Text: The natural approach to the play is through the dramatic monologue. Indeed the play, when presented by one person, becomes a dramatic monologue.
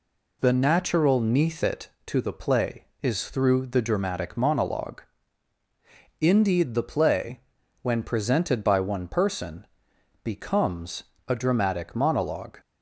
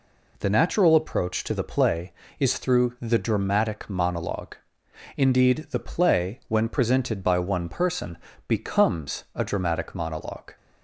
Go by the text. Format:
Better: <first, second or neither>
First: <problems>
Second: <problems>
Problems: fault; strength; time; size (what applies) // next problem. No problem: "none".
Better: second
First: says "neathit" for "approach"; at 1.2 s // pauses between "becomes" and "a"; slight; at 11.0 s; 0.24 s long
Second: none